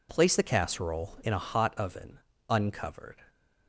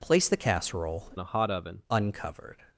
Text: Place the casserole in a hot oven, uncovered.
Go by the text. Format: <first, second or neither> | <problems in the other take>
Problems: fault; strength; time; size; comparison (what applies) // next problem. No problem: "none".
first | changes voice from "in" to "oven"; from 1.1 to 1.8 s; 0.7 s long